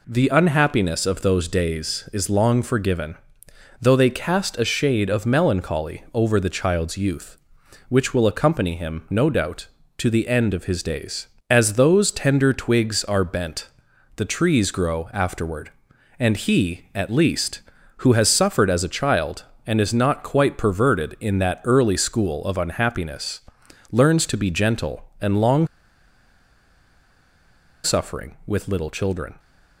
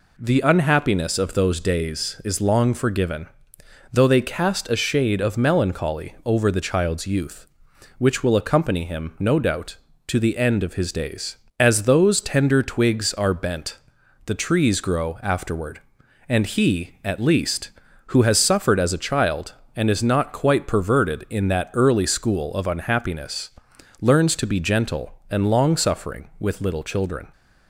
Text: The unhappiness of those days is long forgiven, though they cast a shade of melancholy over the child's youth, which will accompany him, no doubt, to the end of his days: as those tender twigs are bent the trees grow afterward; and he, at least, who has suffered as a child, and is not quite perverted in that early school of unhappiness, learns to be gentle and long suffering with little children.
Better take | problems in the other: second | pauses between "bent" and "the"; noticeable; at 13.6 s; 0.48 s long; noticeable in the second // pauses between "long" and "suffering"; strong; at 25.6 s; 2.1 s long

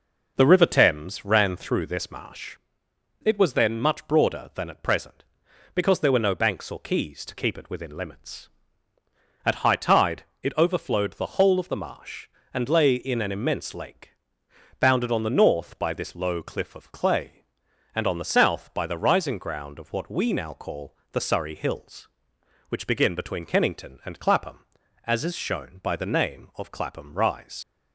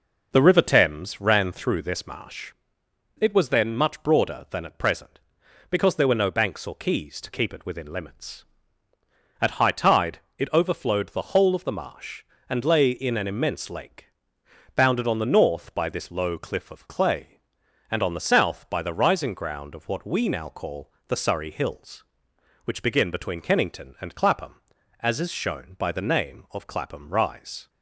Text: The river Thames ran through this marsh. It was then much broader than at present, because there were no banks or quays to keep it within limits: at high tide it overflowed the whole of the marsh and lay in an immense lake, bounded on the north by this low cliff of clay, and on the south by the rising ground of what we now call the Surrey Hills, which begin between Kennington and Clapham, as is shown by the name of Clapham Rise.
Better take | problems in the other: second | pauses between "tide" and "it"; slight; at 10.2 s; 0.18 s long; slight in the second // pauses between "call" and "the"; slight; at 20.9 s; 0.16 s long; slight in the second // leaves "Rise" unfinished; at 27.6 s; 105 ms

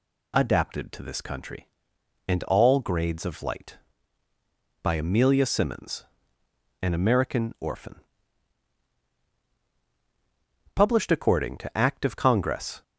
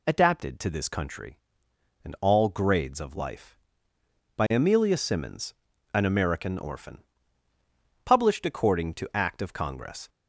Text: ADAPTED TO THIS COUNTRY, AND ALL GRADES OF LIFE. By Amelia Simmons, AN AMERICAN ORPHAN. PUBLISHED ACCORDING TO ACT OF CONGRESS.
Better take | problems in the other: second | says "Light" for "LIFE"; at 3.4 s

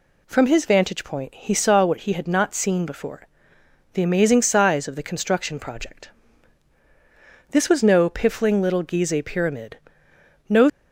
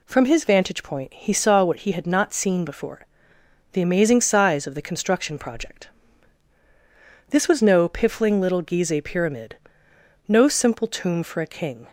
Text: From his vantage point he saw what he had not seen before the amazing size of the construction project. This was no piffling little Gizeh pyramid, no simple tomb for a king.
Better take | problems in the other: second | pauses between "before" and "the"; noticeable; at 3.2 s; 0.66 s long; noticeable in the second // stops before "simple tomb for a king"; at 10.6 s

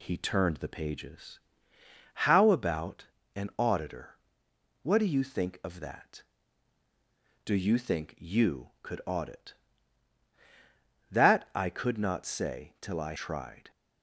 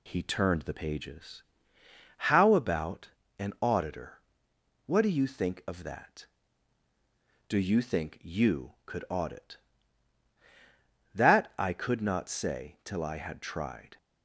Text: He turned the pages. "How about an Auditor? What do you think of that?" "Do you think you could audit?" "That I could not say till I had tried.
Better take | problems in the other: second | pauses between "about" and "an"; slight; at 3.0 s; 0.30 s long; slight in the second // skips "had"; at 13.1 s

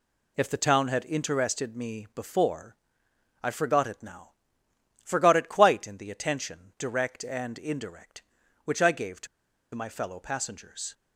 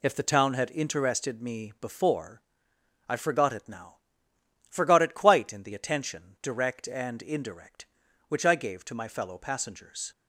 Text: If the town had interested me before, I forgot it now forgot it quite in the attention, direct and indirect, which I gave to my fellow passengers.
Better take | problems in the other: second | pauses between "now" and "forgot"; noticeable; at 4.3 s; 0.72 s long; noticeable in the second // pauses between "to" and "my"; noticeable; at 9.2 s; 0.47 s long

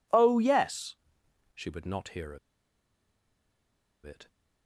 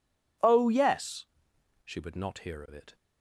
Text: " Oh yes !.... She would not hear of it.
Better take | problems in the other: second | pauses between "of" and "it"; strong; at 2.3 s; 1.6 s long

